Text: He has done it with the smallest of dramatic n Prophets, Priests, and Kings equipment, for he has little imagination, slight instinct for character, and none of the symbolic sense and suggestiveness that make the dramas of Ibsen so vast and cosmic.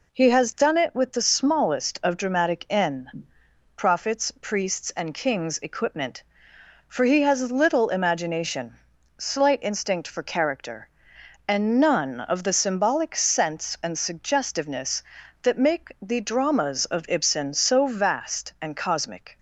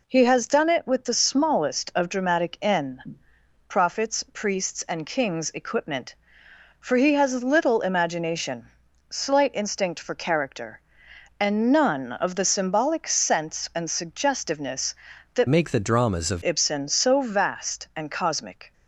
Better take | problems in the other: first | pauses between "n" and "Prophets"; noticeable; at 3.1 s; 0.52 s long; noticeable in the first // changes voice from "make" to "of"; from 15.4 to 16.4 s; 1.0 s long

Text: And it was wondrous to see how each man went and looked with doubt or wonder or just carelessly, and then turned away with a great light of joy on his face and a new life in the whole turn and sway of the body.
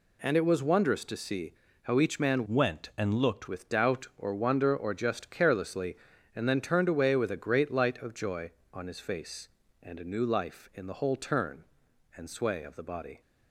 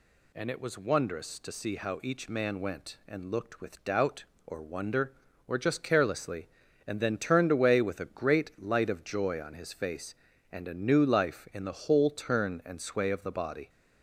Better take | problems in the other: second | pauses between "see" and "how"; slight; at 1.5 s; 0.32 s long // changes voice from "went" to "looked"; from 2.4 to 3.4 s; 1.0 s long

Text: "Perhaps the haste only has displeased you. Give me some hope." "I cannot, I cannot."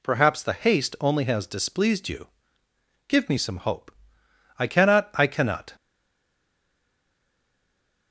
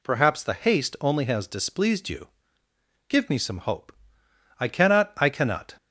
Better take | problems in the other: second | stays silent after the last word; from 5.7 s on; 2.4 s long

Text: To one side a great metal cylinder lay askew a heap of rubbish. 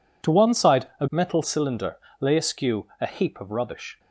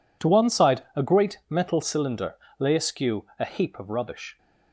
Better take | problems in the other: second | skips "great"; at 1.0 s // pauses between "cylinder" and "lay"; slight; at 1.9 s; 0.24 s long; slight in the second

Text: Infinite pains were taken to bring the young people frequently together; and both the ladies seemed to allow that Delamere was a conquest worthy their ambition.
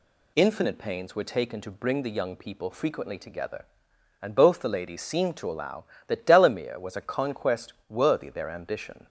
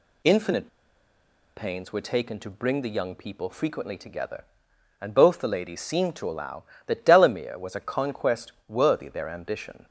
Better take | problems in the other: first | pauses between "Infinite" and "pains"; noticeable; at 0.6 s; 0.90 s long // pauses between "conquest" and "worthy"; slight; at 8.5 s; 0.16 s long; slight in the first

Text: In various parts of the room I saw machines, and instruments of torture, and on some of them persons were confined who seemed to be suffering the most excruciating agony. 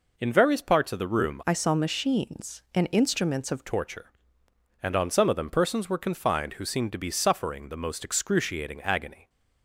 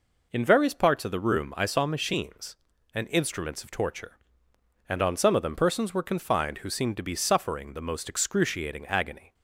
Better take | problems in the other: second | changes voice from "I" to "of"; from 1.4 to 3.6 s; 2.2 s long

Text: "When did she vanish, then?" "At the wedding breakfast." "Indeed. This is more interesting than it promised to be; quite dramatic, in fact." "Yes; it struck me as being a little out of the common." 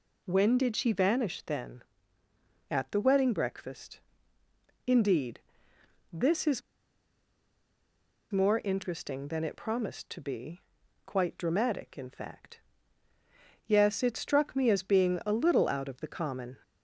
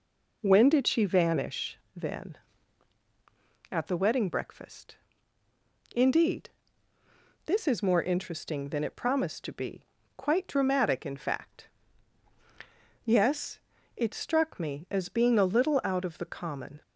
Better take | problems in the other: second | pauses between "is" and "more"; strong; at 6.6 s; 1.7 s long

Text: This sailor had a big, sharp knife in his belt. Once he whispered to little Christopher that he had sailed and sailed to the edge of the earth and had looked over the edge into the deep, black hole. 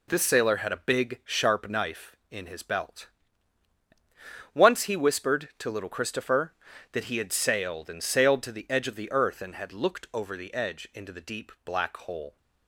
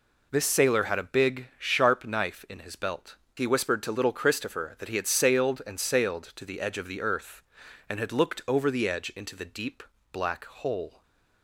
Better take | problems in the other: first | skips "Once"; at 3.2 s

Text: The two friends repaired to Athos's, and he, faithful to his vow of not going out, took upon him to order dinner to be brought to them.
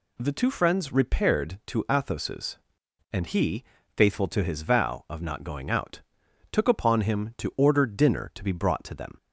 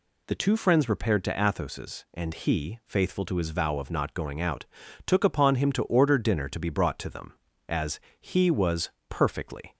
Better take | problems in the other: first | goes on to say "As he was perfectly"; strong; from 7.6 s on; 2.0 s long

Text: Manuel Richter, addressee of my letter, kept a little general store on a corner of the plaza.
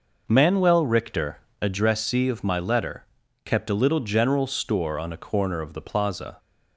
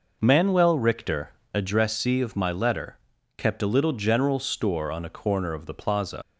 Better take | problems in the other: first | leaves "plaza" unfinished; at 6.2 s; 90 ms

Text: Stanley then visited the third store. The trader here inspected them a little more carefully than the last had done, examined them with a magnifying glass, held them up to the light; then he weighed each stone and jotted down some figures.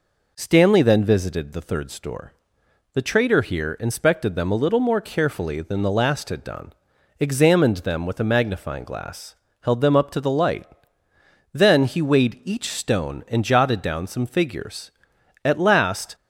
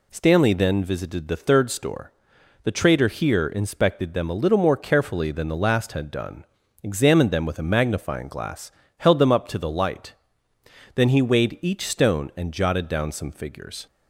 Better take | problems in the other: second | goes on to say "At last"; noticeable; from 15.4 s on; 0.72 s long

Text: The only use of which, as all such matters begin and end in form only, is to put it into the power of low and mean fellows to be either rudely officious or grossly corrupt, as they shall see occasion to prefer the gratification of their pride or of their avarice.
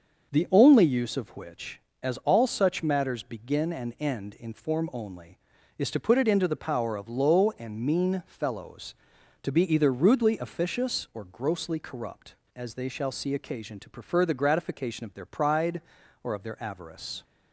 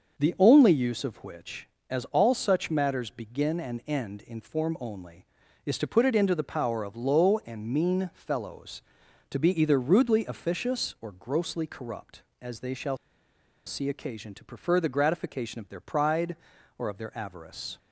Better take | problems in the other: first | starts louder than the rest; until 1.2 s; 6.5 dB; also in the first // pauses between "shall" and "see"; noticeable; at 12.9 s; 0.69 s long

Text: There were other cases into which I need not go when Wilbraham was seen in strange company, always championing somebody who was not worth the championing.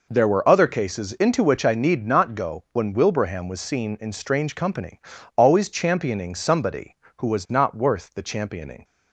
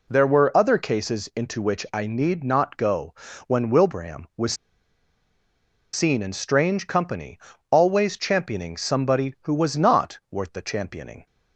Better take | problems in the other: first | pauses between "go" and "when"; slight; at 3.1 s; 0.34 s long // pauses between "was" and "seen"; strong; at 4.5 s; 1.3 s long

